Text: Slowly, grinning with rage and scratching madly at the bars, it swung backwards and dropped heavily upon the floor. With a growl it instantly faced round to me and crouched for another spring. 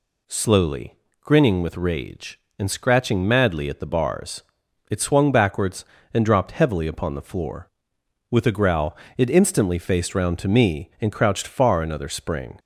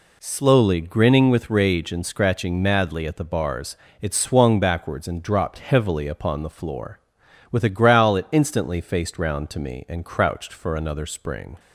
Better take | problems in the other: second | pauses between "growl" and "it"; slight; at 8.9 s; 0.20 s long // says "far" for "for"; at 11.4 s

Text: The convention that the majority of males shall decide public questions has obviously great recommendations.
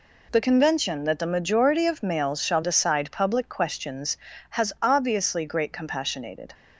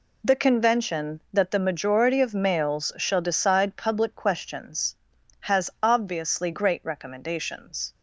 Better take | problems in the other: second | says "compassionated" for "recommendations"; at 5.7 s

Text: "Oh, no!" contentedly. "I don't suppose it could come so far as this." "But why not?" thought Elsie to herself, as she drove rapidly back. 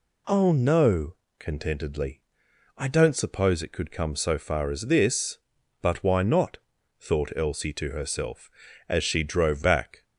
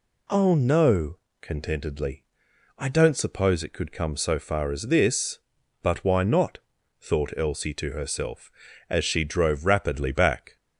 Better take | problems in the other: second | skips "rapidly"; at 9.6 s

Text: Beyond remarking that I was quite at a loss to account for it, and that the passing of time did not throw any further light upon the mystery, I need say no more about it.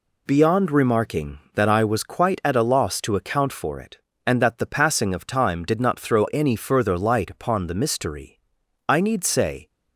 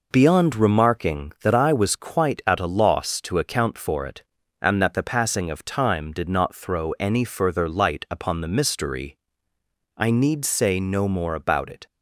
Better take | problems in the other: second | stops before "no more about it"; at 9.6 s

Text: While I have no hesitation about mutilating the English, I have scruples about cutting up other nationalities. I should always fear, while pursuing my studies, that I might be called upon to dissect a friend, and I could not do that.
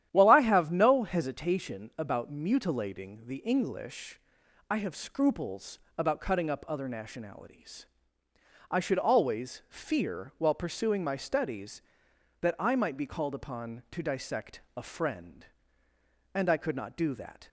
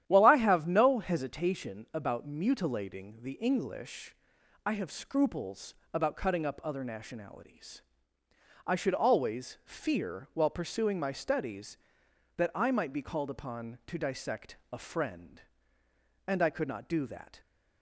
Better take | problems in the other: neither | starts louder than the rest; strong; the same in both // pauses between "scruples" and "about"; slight; the same in both

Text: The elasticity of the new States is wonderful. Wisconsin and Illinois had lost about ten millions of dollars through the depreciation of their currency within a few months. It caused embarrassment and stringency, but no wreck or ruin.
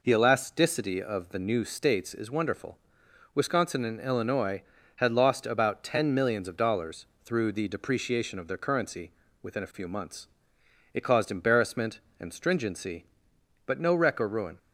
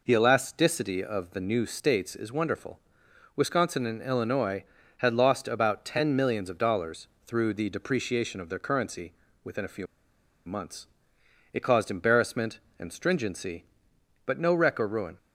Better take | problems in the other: first | pauses between "dollars" and "through"; slight; at 7.0 s; 0.20 s long; slight in the first // pauses between "currency" and "within"; slight; at 9.1 s; 0.30 s long; slight in the first // pauses between "few" and "months"; noticeable; at 9.8 s; 0.61 s long

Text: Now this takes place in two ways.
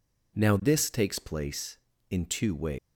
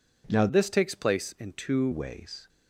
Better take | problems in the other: first | changes voice from "this" to "two"; from 0.4 to 1.8 s; 1.4 s long

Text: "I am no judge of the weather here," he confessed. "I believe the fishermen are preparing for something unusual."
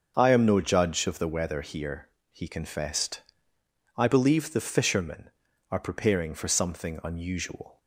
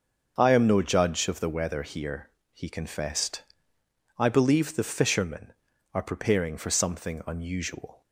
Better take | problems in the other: neither | starts louder than the rest; the same in both

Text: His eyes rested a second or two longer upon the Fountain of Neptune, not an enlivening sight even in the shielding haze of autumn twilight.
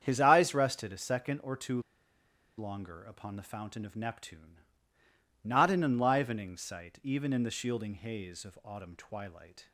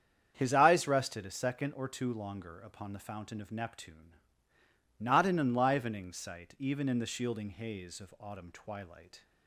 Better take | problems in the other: second | starts louder than the rest; strong; until 1.0 s; 8 dB; strong in the second // pauses between "two" and "longer"; noticeable; at 1.8 s; 0.77 s long

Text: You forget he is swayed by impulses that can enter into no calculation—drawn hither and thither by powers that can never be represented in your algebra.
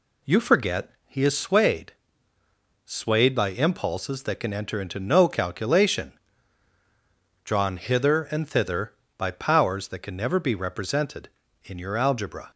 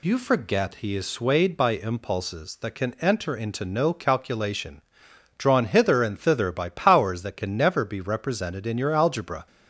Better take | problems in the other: second | pauses between "forget" and "he"; slight; at 0.9 s; 0.16 s long // says "swayed" twice; at 2.8 s

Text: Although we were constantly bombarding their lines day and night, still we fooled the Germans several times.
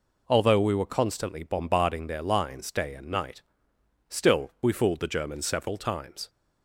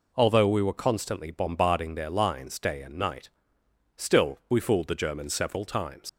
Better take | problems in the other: first | leaves "times" unfinished; at 6.0 s; 70 ms

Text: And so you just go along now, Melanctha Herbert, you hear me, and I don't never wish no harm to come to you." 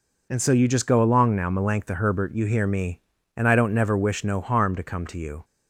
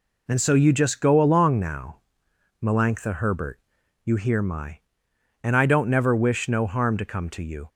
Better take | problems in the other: first | says "my" for "me"; at 4.4 s

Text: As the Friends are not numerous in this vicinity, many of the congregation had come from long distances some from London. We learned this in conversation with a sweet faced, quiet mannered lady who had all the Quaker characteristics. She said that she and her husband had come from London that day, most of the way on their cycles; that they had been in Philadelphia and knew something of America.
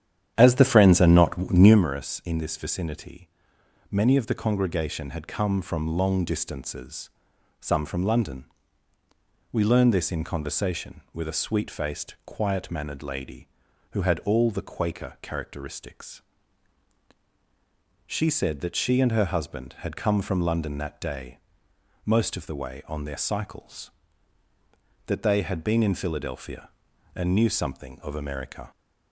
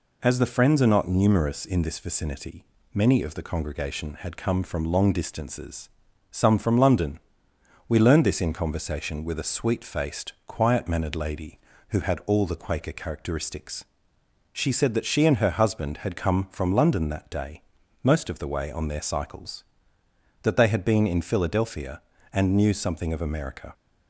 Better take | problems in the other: second | starts louder than the rest; strong; until 1.8 s; 9.5 dB // pauses between "distances" and "some"; noticeable; at 7.1 s; 0.50 s long; also in the second

